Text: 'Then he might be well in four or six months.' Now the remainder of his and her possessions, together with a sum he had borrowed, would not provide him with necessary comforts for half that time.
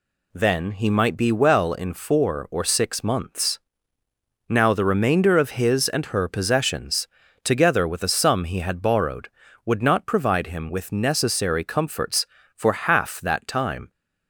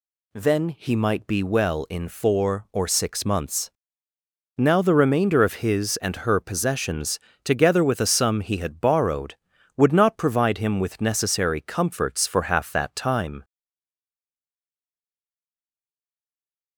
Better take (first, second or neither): first